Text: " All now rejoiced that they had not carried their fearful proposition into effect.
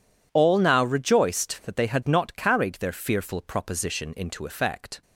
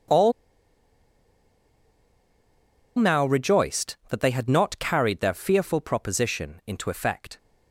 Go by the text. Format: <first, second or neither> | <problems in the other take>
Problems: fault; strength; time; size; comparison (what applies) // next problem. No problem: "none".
first | pauses between "All" and "now"; strong; at 0.3 s; 2.6 s long